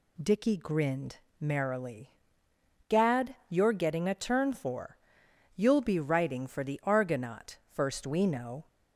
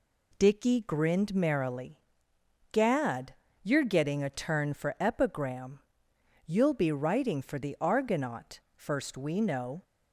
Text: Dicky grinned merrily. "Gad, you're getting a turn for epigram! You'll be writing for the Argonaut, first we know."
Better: second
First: pauses between "grinned" and "merrily"; slight; at 1.1 s; 0.22 s long // skips "epigram"; at 5.2 s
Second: none

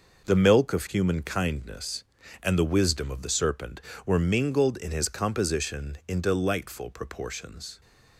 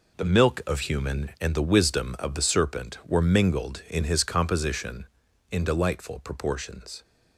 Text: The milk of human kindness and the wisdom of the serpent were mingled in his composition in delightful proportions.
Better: first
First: none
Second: skips "kindness"; at 1.3 s

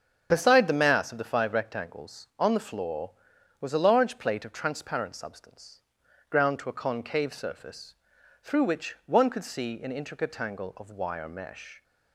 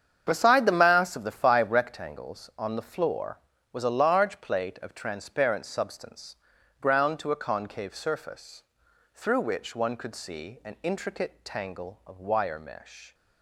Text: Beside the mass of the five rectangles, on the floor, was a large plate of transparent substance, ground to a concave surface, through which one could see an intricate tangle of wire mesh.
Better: neither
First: starts louder than the rest; until 1.3 s; 7 dB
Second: starts louder than the rest; strong; until 1.2 s; 8 dB

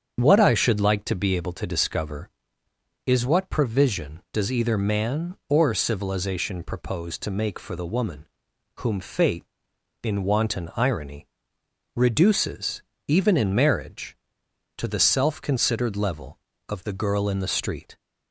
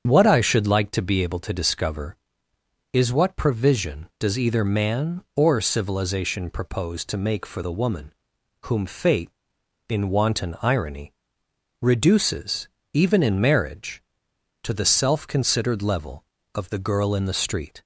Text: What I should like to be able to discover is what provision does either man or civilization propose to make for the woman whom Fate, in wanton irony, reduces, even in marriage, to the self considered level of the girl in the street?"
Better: neither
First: starts louder than the rest; strong; until 1.2 s; 7.5 dB // pauses between "woman" and "whom"; noticeable; at 8.2 s; 0.52 s long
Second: starts louder than the rest; strong; until 1.0 s; 7.5 dB // pauses between "woman" and "whom"; noticeable; at 8.1 s; 0.52 s long

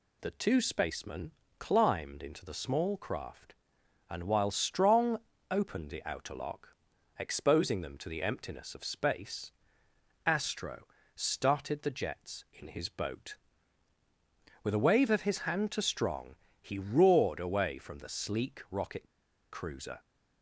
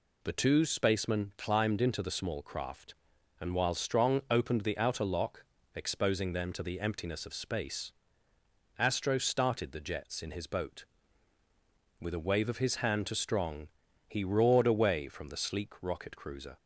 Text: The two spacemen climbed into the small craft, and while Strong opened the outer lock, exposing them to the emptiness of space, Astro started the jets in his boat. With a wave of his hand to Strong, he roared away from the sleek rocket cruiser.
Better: second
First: pauses between "spacemen" and "climbed"; slight; at 1.3 s; 0.28 s long // pauses between "Strong" and "opened"; slight; at 5.1 s; 0.30 s long // pauses between "Astro" and "started"; slight; at 10.8 s; 0.32 s long // pauses between "rocket" and "cruiser"; at 19.0 s; 0.45 s long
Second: none

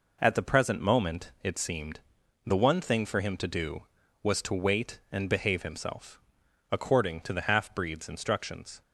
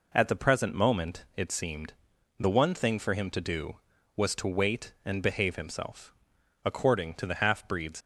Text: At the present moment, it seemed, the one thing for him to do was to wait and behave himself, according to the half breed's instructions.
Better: first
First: none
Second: stops before "instructions"; at 8.0 s

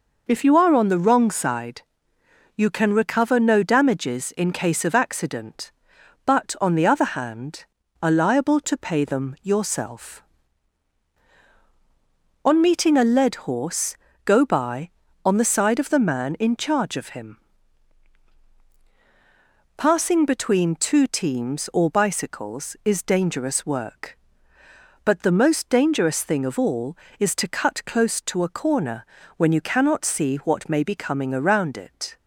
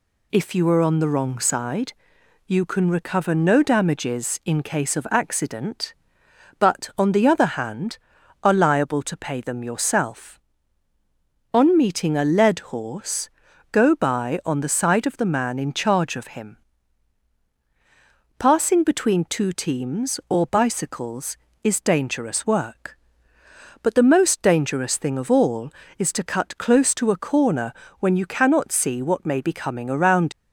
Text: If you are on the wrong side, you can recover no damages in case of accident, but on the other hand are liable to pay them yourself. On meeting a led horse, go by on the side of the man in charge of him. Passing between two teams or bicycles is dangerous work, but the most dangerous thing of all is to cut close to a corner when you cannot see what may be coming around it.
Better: first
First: pauses between "corner" and "when"; slight; at 29.0 s; 0.32 s long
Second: pauses between "corner" and "when"; slight; at 27.7 s; 0.28 s long // stops before "it"; at 30.3 s

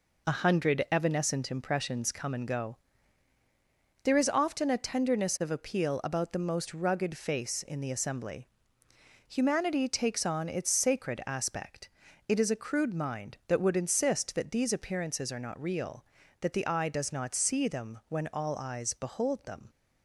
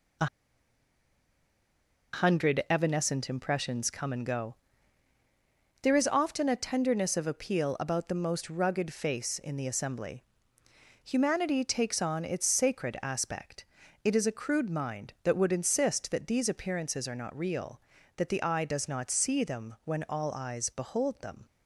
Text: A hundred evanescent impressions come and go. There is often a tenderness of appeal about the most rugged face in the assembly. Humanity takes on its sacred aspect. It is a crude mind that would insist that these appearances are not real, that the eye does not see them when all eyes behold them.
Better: first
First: none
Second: pauses between "A" and "hundred"; strong; at 0.2 s; 1.8 s long

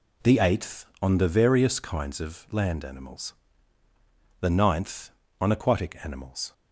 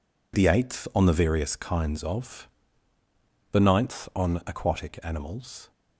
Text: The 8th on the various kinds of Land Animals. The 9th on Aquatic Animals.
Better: first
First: none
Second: skips "Land Animals"; at 3.0 s

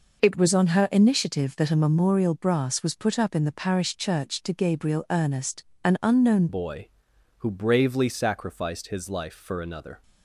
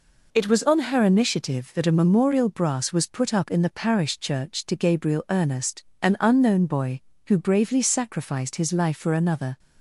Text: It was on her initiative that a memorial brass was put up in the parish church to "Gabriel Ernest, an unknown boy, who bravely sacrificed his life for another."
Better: second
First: changes voice at "boy"; from 6.4 s on; 3.6 s long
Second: none

